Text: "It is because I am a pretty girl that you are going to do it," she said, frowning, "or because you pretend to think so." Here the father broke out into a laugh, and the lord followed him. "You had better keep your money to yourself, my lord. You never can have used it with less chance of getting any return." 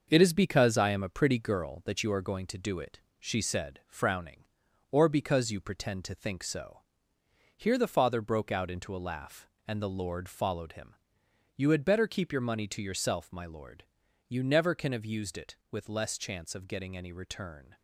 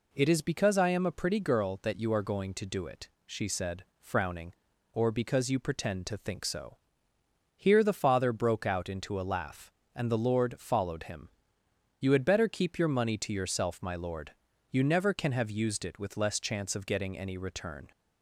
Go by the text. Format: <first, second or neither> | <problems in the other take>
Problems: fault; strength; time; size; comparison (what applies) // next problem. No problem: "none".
second | gets quieter; noticeable; throughout; 5.5 dB